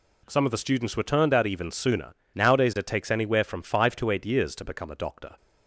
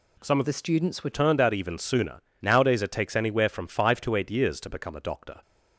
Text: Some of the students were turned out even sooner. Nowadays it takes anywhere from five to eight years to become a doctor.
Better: first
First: none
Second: changes voice from "the" to "were"; from 0.4 to 1.0 s; 0.6 s long

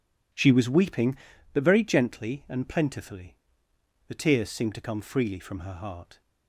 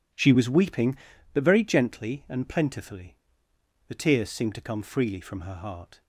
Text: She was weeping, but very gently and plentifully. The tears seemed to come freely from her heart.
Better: neither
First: none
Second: none

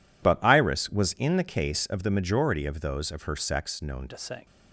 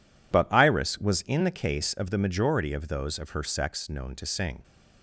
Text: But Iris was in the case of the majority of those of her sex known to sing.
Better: second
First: changes voice at "to"; from 4.0 s on; 0.4 s long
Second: none

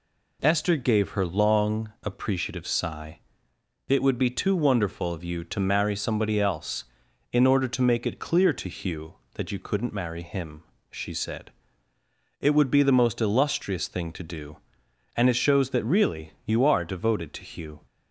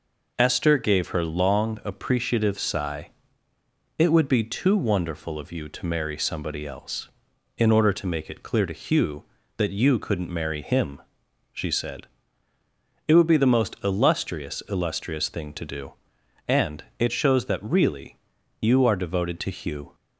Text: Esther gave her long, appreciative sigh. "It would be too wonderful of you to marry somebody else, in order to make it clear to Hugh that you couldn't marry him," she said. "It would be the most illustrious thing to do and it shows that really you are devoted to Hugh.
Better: first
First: none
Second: says "illustrious" twice; at 14.6 s // pauses between "and" and "it"; slight; at 16.8 s; 0.16 s long // pauses between "really" and "you"; at 18.1 s; 0.42 s long

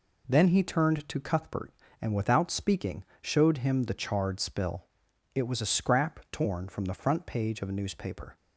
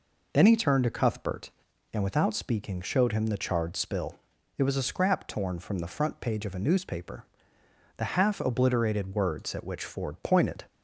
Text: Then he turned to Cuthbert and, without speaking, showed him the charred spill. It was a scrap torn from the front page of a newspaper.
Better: first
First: none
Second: goes on to say "The half obliterated words at which Ford pointed"; strong; from 7.9 s on; 2.6 s long

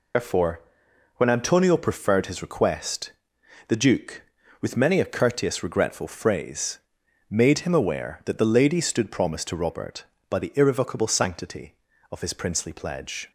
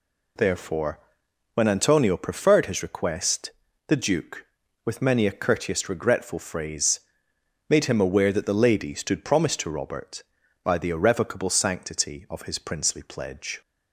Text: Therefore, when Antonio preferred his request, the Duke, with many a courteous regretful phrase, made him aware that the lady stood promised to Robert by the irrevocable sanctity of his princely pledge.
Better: second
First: loses the start of "Therefore"; at 0.1 s; 125 ms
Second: none

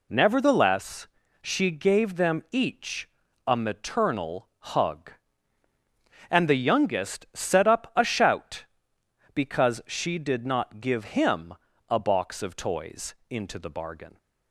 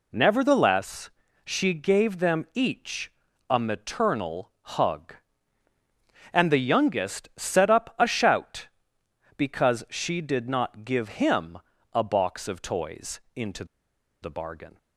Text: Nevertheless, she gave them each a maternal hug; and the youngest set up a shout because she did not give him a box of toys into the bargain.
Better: first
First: pauses between "each" and "a"; at 3.0 s; 0.38 s long // pauses between "him" and "a"; slight; at 11.5 s; 0.34 s long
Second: pauses between "each" and "a"; at 3.1 s; 0.38 s long // pauses between "him" and "a"; slight; at 11.5 s; 0.34 s long // pauses between "into" and "the"; noticeable; at 13.6 s; 0.57 s long

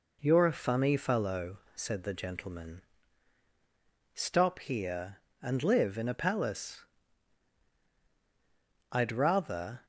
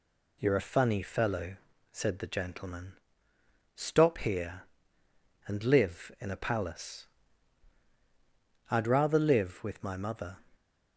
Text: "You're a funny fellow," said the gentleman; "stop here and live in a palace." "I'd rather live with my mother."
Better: second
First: stops before "live with my mother"; at 9.8 s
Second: none

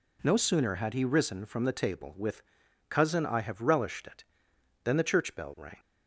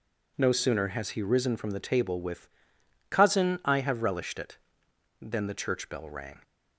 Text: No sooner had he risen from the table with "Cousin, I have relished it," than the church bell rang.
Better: first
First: pauses between "with" and "Cousin"; noticeable; at 2.4 s; 0.48 s long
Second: says "has" for "had"; at 0.8 s // pauses between "with" and "Cousin"; noticeable; at 2.4 s; 0.62 s long

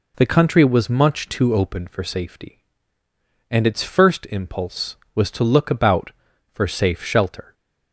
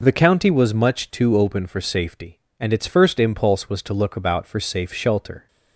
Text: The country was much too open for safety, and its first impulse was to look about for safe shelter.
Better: first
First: none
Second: says "county" for "country"; at 0.2 s

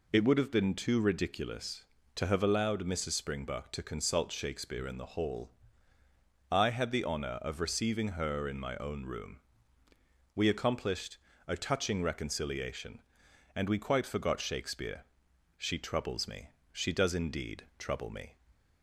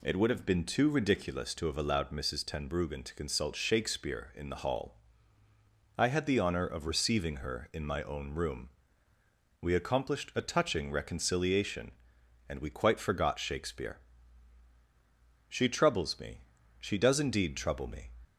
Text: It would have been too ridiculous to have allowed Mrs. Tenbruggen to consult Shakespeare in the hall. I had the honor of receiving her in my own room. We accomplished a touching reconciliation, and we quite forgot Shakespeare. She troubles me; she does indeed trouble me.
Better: second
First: says "Springbuck" for "Tenbruggen"; at 3.1 s // pauses between "accomplished" and "a"; slight; at 11.1 s; 0.28 s long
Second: none

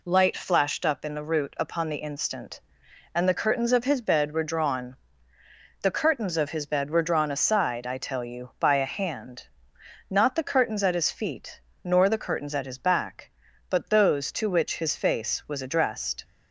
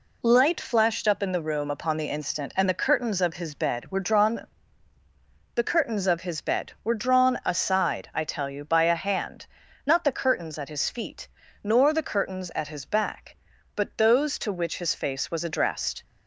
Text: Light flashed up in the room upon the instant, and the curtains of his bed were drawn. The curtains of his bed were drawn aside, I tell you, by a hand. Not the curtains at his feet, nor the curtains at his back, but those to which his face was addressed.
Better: second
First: says "root" for "room"; at 1.2 s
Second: none

